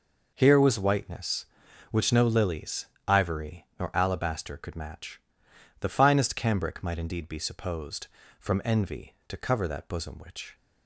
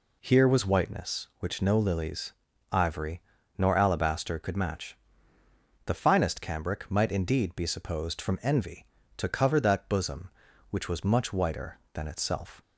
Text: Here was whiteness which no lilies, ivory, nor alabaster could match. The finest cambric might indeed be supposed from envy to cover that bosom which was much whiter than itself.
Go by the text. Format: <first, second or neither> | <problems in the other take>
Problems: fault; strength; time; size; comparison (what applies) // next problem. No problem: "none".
second | stops before "was much whiter than itself"; at 10.5 s